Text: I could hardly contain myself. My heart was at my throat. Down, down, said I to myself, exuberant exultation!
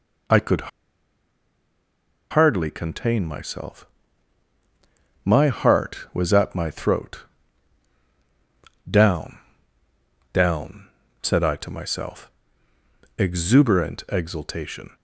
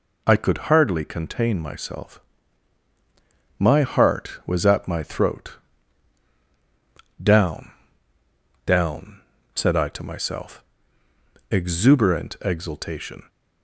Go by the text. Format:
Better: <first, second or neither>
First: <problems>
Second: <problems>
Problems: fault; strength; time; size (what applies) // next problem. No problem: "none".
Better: second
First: pauses between "could" and "hardly"; strong; at 0.6 s; 1.6 s long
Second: none